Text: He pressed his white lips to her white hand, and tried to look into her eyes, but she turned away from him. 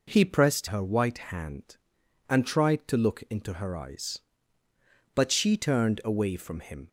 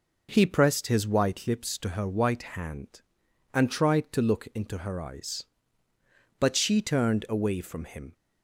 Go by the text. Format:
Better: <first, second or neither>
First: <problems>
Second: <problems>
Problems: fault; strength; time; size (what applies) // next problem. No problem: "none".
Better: second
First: skips "his white lips to"; at 0.6 s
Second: none